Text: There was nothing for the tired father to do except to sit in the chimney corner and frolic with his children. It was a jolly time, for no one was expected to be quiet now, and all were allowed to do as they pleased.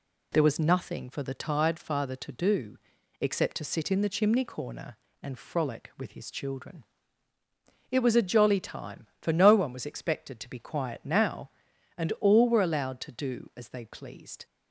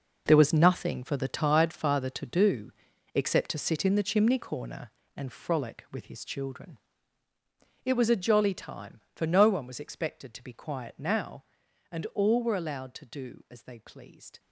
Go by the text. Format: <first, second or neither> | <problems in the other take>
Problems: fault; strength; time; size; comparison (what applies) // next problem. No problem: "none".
first | gets quieter; strong; throughout; 13 dB // pauses between "do" and "except"; at 2.7 s; 0.44 s long; also in the first